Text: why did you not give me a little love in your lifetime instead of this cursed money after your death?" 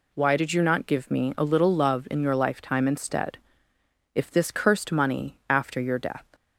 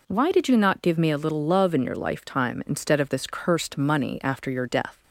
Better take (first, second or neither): second